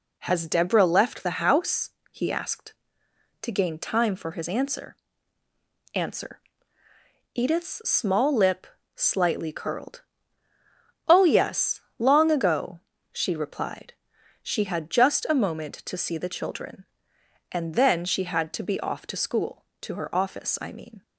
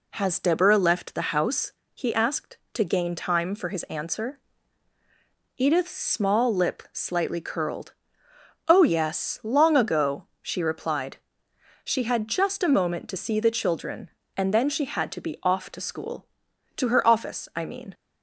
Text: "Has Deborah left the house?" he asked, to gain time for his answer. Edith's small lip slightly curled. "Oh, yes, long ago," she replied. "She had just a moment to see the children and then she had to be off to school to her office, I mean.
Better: second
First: says "answer" twice; at 5.9 s // pauses between "lip" and "slightly"; slight; at 8.6 s; 0.30 s long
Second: none

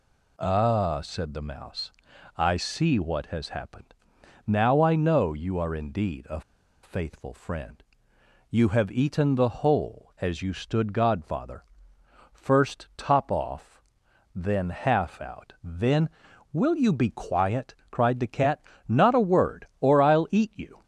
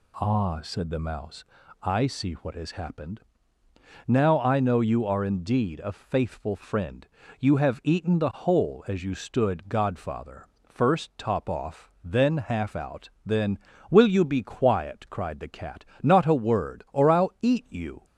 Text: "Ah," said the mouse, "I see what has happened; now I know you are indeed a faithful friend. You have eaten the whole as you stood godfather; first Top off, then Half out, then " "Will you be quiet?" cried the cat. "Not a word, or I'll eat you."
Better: second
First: pauses between "a" and "faithful"; at 6.4 s; 0.42 s long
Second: none

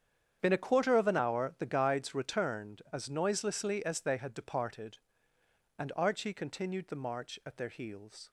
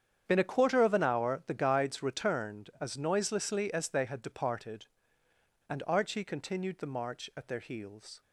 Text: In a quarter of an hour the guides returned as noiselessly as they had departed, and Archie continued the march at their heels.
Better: neither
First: starts louder than the rest; strong; until 1.4 s; 8.5 dB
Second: starts louder than the rest; strong; until 1.2 s; 8.5 dB

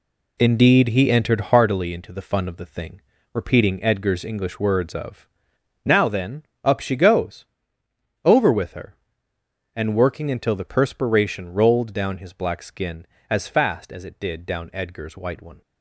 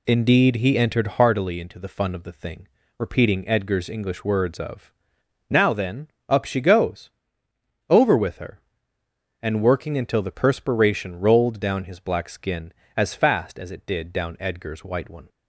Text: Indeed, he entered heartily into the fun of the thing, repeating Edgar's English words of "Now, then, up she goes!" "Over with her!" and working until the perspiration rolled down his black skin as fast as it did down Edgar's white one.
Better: second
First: gets quieter; strong; throughout; 8.5 dB // pauses between "of" and "Now"; noticeable; at 5.2 s; 0.56 s long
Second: pauses between "of" and "Now"; noticeable; at 4.9 s; 0.56 s long

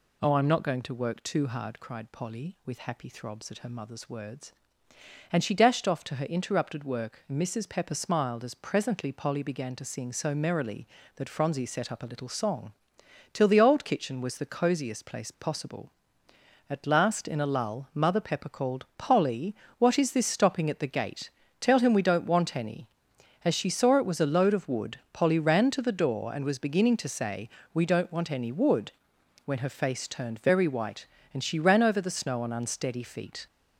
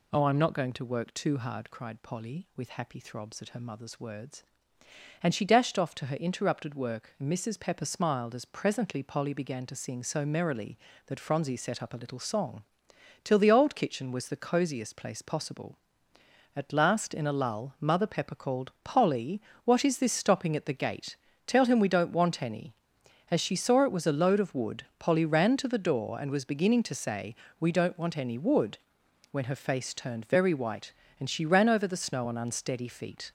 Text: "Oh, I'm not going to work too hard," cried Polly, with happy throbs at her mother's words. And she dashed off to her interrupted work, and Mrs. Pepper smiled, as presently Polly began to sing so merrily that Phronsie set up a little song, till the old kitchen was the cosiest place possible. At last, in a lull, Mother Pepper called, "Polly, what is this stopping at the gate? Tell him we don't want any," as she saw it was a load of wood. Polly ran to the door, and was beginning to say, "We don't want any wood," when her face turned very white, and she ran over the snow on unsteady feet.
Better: neither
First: none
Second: none

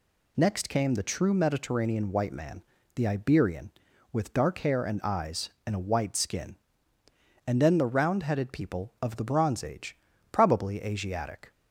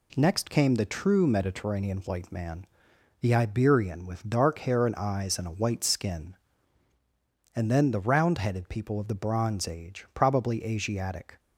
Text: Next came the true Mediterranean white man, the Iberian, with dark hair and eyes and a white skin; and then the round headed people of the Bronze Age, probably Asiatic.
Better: neither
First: none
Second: none

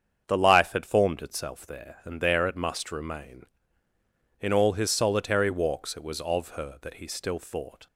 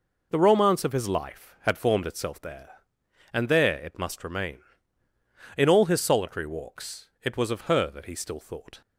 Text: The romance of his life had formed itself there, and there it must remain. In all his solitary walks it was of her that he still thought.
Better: second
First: starts louder than the rest; strong; until 1.2 s; 7.5 dB // skips "romance of his"; at 0.3 s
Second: none

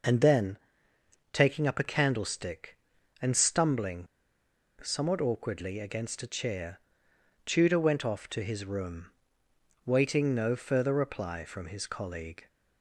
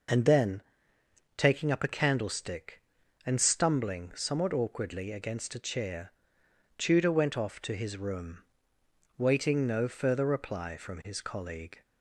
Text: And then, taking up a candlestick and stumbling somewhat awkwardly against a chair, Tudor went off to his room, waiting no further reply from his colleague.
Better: second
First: pauses between "stumbling" and "somewhat"; noticeable; at 4.0 s; 0.76 s long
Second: none

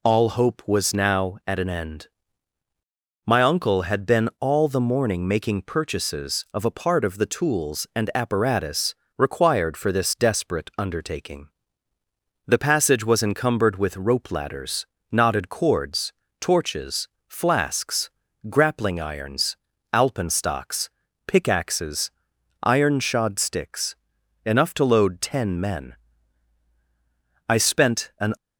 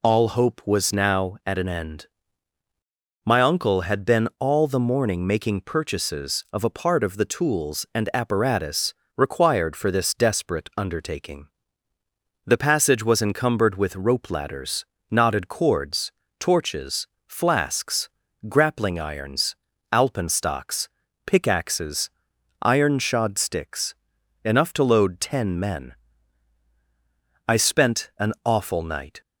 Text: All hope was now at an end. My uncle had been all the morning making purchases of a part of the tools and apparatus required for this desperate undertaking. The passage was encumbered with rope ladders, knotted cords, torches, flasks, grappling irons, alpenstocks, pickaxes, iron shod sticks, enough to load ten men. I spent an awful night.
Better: second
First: pauses between "apparatus" and "required"; slight; at 8.9 s; 0.20 s long // stops before "awful night"; at 28.3 s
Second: pauses between "apparatus" and "required"; slight; at 8.9 s; 0.20 s long

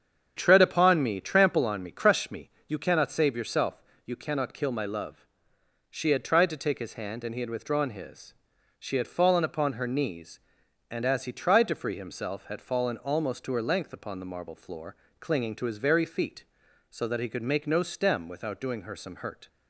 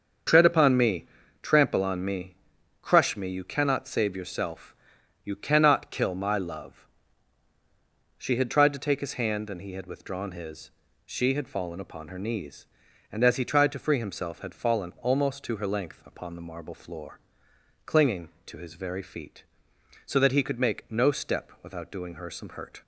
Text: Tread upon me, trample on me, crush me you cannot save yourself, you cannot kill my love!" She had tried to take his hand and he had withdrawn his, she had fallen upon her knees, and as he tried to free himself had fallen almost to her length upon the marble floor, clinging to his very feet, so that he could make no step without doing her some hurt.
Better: second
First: starts louder than the rest; strong; until 1.3 s; 8 dB // pauses between "me" and "you"; slight; at 2.4 s; 0.18 s long // says "stem" for "step"; at 17.8 s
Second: starts louder than the rest; until 1.6 s; 7 dB

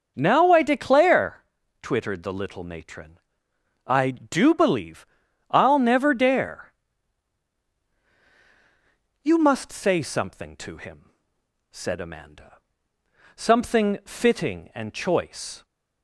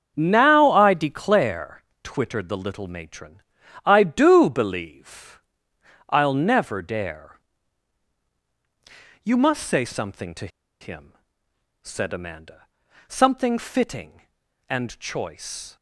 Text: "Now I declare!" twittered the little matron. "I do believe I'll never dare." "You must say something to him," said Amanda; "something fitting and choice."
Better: first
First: starts louder than the rest; until 1.1 s; 6.5 dB // pauses between "believe" and "I'll"; at 5.0 s; 0.42 s long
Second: starts louder than the rest; until 1.1 s; 7 dB // pauses between "believe" and "I'll"; noticeable; at 5.3 s; 0.70 s long // pauses between "to" and "him"; slight; at 10.4 s; 0.33 s long

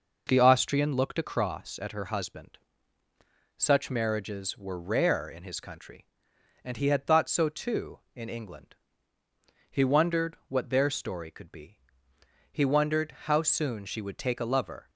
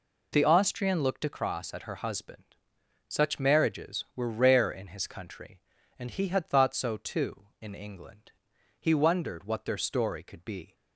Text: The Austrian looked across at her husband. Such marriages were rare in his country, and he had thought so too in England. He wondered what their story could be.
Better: second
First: goes on to say "He wondered how soon she would take a lover"; strong; from 12.5 s on; 2.3 s long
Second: none

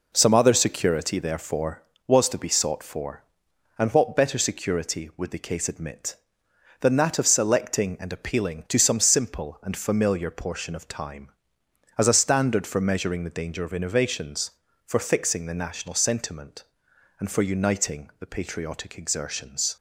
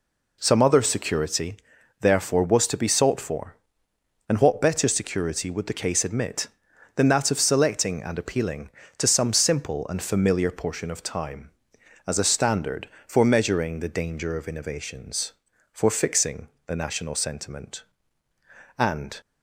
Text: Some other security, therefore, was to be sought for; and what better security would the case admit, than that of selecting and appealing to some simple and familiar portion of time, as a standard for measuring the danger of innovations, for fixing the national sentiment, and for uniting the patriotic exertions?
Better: first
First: none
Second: pauses between "fixing" and "the"; slight; at 16.4 s; 0.22 s long // stops before "for uniting the patriotic exertions"; at 19.2 s

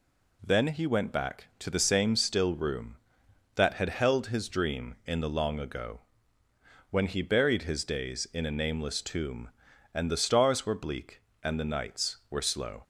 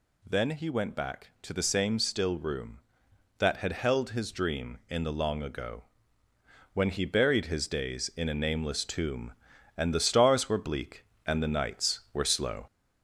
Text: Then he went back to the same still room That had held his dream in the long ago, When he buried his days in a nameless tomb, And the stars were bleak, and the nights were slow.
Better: first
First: none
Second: gets louder; slight; throughout; 2.5 dB

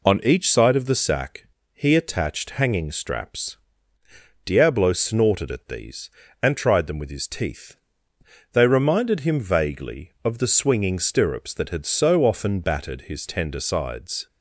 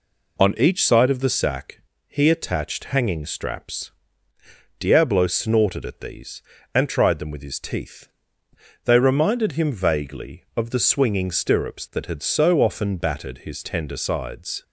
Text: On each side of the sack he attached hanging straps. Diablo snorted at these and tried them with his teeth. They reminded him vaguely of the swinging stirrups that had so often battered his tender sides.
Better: neither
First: pauses between "sack" and "he"; slight; at 1.4 s; 0.28 s long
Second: pauses between "sack" and "he"; slight; at 1.8 s; 0.28 s long

